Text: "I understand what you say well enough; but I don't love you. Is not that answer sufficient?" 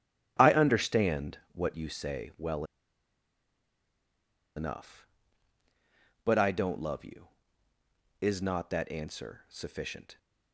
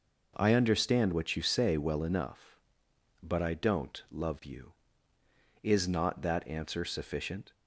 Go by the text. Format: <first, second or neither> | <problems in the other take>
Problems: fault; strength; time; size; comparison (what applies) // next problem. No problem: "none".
second | starts louder than the rest; strong; until 1.4 s; 12 dB // pauses between "well" and "enough"; strong; at 2.6 s; 1.9 s long